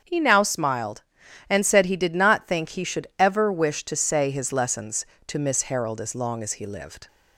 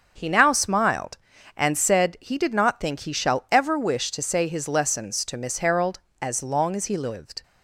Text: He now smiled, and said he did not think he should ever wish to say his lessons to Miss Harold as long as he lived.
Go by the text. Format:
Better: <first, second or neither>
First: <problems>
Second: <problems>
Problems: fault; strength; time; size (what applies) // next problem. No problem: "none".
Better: first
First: starts louder than the rest; until 1.5 s; 7 dB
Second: starts louder than the rest; until 1.1 s; 6.5 dB // says "shall" for "should"; at 3.1 s